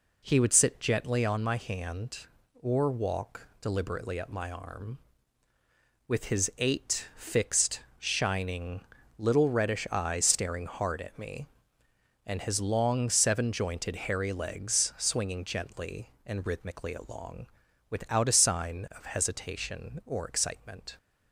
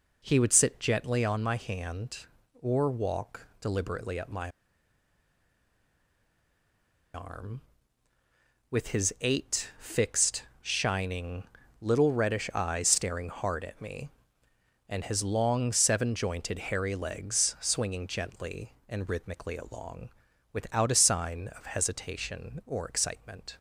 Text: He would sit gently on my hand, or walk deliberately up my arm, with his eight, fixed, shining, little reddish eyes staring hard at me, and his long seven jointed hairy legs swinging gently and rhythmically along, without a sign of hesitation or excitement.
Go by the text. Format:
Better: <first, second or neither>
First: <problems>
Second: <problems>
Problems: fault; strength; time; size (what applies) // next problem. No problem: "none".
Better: first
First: none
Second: pauses between "my" and "arm"; strong; at 4.4 s; 2.6 s long